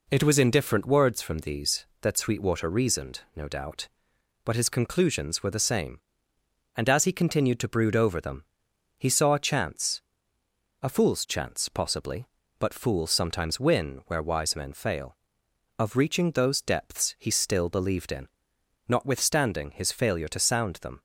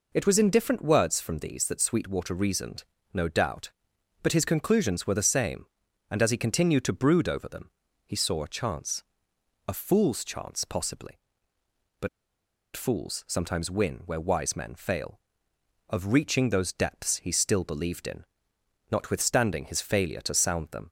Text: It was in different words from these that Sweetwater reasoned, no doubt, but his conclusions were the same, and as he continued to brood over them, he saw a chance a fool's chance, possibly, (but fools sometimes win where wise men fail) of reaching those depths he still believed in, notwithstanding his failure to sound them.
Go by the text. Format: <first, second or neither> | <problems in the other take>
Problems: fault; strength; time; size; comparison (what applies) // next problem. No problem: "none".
first | pauses between "chance" and "a"; noticeable; at 9.0 s; 0.68 s long; noticeable in the first // pauses between "but" and "fools"; noticeable; at 12.0 s; 0.65 s long